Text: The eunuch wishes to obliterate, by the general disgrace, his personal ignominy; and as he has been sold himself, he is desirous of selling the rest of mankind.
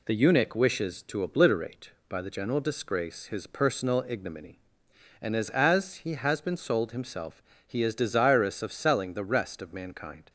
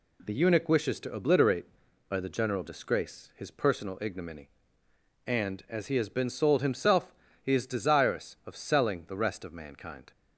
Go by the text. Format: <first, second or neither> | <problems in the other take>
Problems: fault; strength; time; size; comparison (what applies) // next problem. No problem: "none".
second | says "as" twice; at 5.4 s